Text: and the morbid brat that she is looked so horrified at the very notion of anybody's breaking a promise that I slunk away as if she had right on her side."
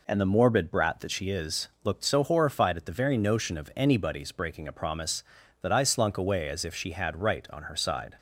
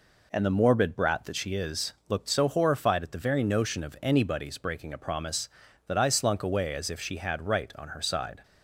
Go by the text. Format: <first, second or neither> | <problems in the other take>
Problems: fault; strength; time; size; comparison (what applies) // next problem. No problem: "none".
neither | none